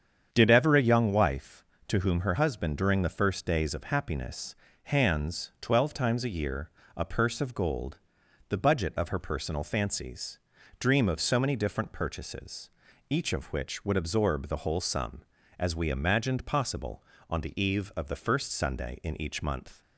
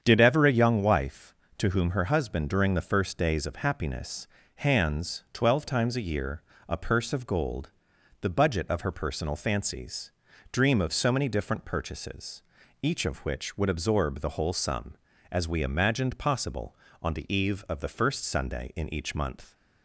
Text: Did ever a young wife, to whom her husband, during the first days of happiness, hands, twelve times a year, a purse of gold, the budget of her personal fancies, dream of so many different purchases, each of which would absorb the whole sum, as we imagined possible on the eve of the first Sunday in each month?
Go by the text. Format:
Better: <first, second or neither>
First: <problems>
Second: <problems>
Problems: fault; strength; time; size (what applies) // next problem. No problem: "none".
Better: neither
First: starts louder than the rest; strong; until 1.3 s; 8 dB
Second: starts louder than the rest; strong; until 1.0 s; 8 dB